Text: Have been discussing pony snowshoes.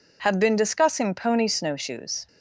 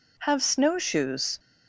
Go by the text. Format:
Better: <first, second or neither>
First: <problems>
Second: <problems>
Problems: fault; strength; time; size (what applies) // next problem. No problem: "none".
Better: first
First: none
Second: skips "been discussing pony"; at 0.4 s